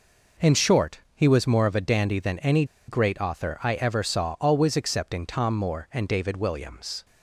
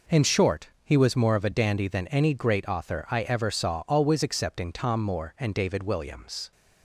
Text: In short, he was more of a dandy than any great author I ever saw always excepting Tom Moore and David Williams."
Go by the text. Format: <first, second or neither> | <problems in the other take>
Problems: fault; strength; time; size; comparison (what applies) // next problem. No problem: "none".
second | pauses between "any" and "great"; slight; at 2.6 s; 0.24 s long